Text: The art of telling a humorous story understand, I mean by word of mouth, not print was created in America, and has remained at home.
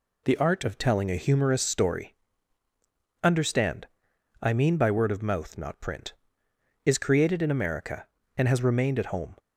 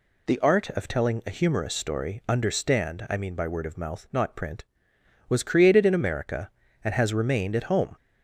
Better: second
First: pauses between "story" and "understand"; at 2.1 s; 1.1 s long // says "is" for "was"; at 6.8 s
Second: none

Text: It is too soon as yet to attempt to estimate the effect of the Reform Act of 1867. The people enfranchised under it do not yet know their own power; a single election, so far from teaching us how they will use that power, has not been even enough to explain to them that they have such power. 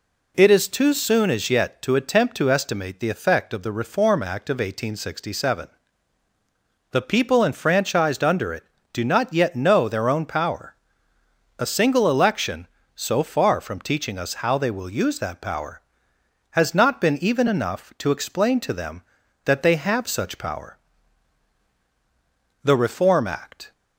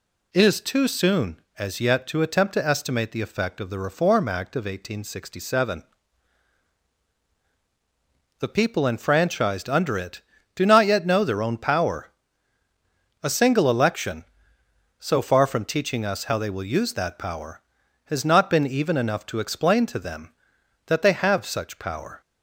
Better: second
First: goes on to say "The Reform Act"; noticeable; from 22.6 s on; 1.1 s long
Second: none

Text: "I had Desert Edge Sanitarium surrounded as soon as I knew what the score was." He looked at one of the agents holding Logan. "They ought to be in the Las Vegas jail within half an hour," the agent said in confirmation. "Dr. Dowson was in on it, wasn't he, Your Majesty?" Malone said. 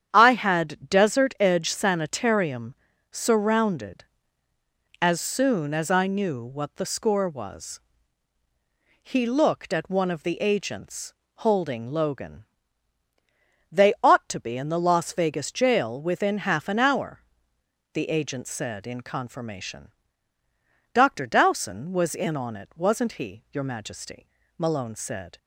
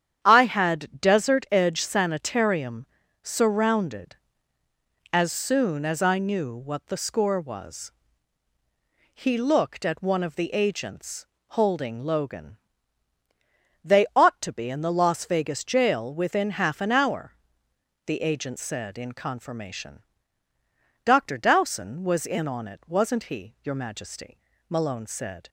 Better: neither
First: starts louder than the rest; strong; until 1.1 s; 9 dB // pauses between "Sanitarium" and "surrounded"; slight; at 2.7 s; 0.36 s long // pauses between "agents" and "holding"; slight; at 11.1 s; 0.22 s long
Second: starts louder than the rest; strong; until 1.2 s; 9 dB // pauses between "Sanitarium" and "surrounded"; slight; at 2.8 s; 0.36 s long // pauses between "agents" and "holding"; slight; at 11.2 s; 0.22 s long

